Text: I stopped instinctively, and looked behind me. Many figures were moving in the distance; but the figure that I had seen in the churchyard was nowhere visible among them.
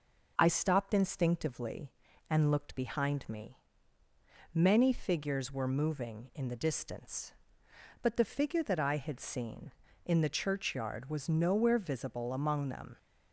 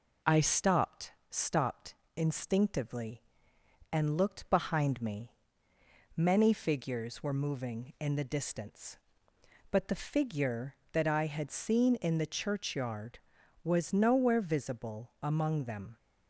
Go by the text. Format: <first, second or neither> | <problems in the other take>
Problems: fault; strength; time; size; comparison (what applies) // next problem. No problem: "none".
first | says "stopped" twice; at 1.3 s